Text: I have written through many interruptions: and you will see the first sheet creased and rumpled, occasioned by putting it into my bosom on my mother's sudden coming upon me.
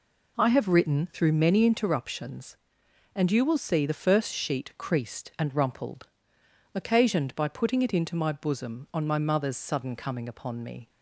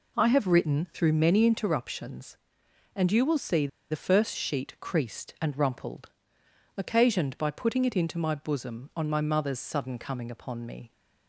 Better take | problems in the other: first | pauses between "see" and "the"; slight; at 3.6 s; 0.23 s long

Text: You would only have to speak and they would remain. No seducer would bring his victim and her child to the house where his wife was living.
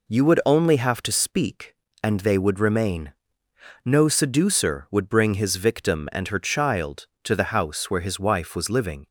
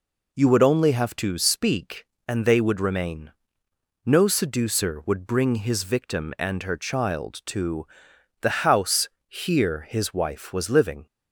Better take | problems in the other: first | pauses between "to" and "the"; noticeable; at 7.8 s; 0.54 s long // says "here" for "where"; at 9.2 s

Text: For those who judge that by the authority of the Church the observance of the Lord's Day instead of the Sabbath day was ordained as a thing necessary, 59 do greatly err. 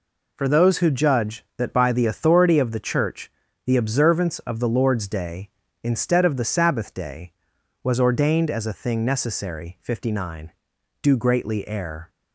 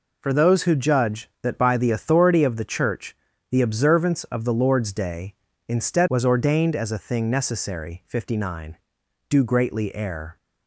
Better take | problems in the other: first | pauses between "Church" and "the"; slight; at 3.1 s; 0.34 s long; slight in the first // skips "of the Sabbath day"; at 6.0 s

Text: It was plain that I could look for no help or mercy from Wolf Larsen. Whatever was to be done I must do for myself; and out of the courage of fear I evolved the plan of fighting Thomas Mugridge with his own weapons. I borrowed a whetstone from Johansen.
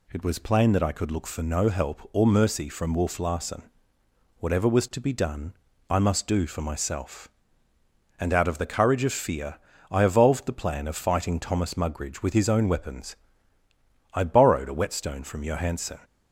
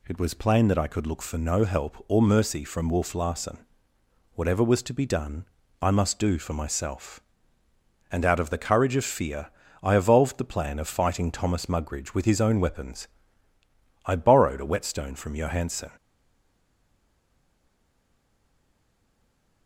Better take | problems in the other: first | pauses between "done" and "I"; slight; at 5.4 s; 0.34 s long; slight in the first // pauses between "fear" and "I"; slight; at 9.4 s; 0.30 s long; slight in the first // stays silent after the last word; strong; from 15.9 s on; 3.7 s long

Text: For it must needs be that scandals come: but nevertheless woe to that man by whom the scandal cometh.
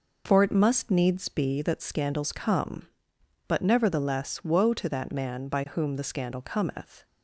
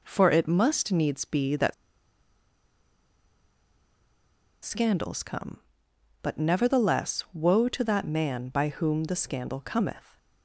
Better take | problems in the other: first | pauses between "that" and "scandals"; strong; at 1.7 s; 2.9 s long

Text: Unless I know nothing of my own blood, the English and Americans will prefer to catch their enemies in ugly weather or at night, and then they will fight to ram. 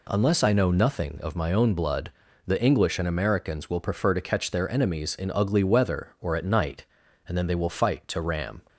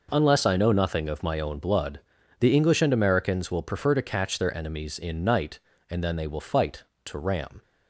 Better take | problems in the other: first | skips "ugly weather or at"; at 5.2 s

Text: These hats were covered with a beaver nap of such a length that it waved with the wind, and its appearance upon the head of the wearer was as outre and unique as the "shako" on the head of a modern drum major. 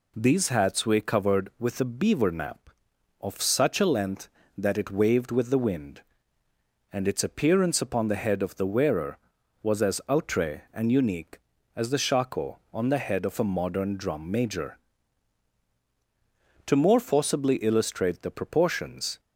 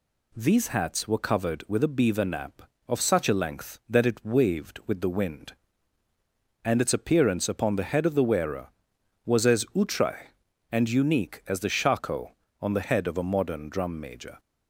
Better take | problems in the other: second | goes on to say "To more forcibly illustrate the proportions"; strong; from 16.6 s on; 2.5 s long

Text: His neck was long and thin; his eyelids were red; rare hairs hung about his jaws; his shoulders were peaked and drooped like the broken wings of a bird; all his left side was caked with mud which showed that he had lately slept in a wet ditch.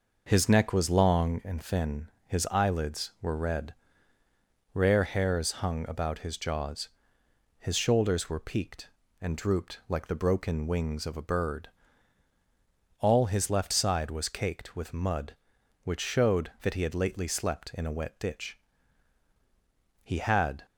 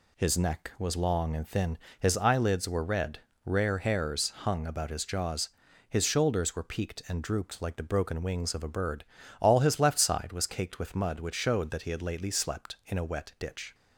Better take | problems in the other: second | goes on to say "He had"; noticeable; from 20.0 s on; 0.62 s long

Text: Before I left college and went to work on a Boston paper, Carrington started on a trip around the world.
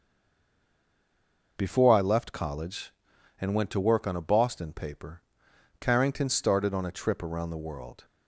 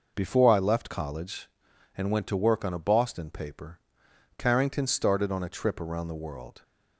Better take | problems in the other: second | stays silent before the first word; noticeable; until 1.5 s; 1.5 s long

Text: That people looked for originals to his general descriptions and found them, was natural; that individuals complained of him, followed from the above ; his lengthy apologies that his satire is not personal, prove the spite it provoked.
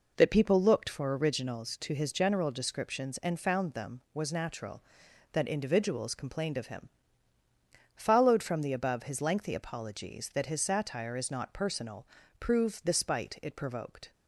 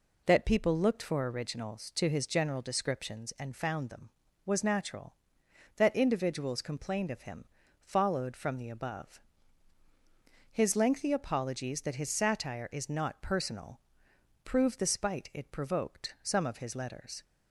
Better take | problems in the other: first | goes on to say "Some of his letters"; noticeable; from 16.2 s on; 1.0 s long

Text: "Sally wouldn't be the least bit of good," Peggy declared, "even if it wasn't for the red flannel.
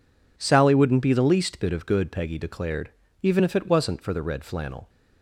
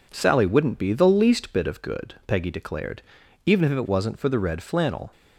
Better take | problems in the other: neither | none

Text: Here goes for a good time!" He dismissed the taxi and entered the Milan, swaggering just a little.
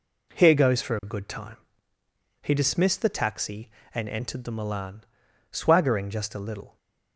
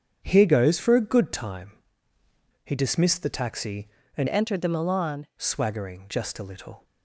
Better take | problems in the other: first | starts louder than the rest; strong; until 1.2 s; 8.5 dB // changes voice from "entered" to "Milan"; from 4.2 to 5.2 s; 1.0 s long

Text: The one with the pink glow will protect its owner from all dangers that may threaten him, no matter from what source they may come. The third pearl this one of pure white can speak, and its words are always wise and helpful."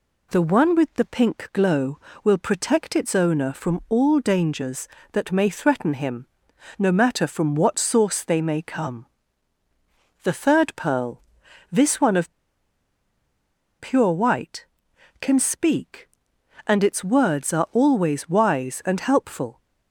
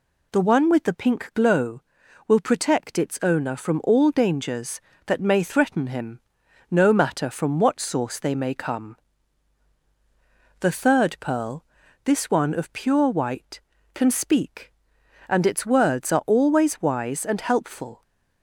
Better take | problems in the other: second | pauses between "pearl" and "this"; noticeable; at 11.2 s; 0.50 s long; also in the second // pauses between "of" and "pure"; strong; at 12.3 s; 1.4 s long

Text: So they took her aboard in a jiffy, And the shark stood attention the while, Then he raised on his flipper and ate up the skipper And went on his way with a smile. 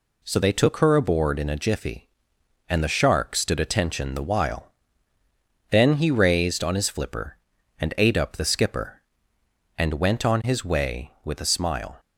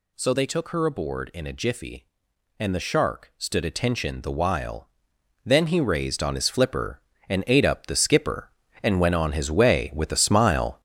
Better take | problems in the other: first | gets louder; throughout; 6.5 dB

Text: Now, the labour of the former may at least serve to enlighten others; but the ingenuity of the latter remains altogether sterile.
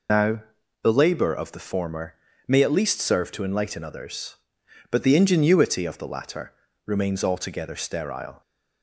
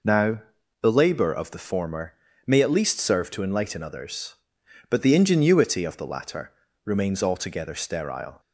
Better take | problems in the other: second | loses the start of "Now"; at 0.0 s; 50 ms // pauses between "former" and "may"; slight; at 2.1 s; 0.32 s long; slight in the second // pauses between "latter" and "remains"; slight; at 6.5 s; 0.34 s long; slight in the second

